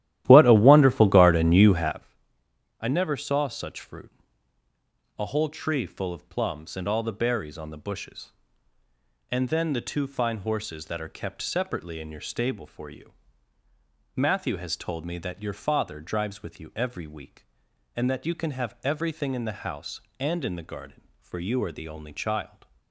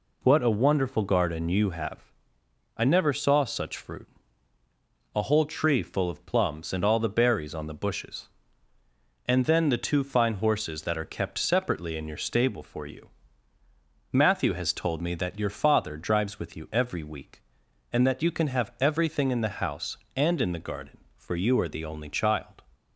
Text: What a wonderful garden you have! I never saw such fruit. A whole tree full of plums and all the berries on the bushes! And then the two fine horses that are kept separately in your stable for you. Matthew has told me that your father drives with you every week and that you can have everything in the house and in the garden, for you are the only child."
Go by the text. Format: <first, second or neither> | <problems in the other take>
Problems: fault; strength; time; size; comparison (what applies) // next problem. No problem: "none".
second | starts louder than the rest; strong; until 2.0 s; 13.5 dB